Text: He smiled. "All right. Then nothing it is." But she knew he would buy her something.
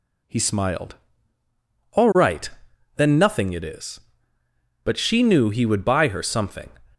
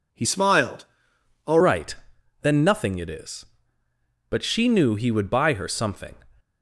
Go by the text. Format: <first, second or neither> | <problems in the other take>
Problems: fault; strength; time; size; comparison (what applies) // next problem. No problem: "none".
first | changes voice from "smiled" to "All"; from 0.2 to 1.5 s; 1.3 s long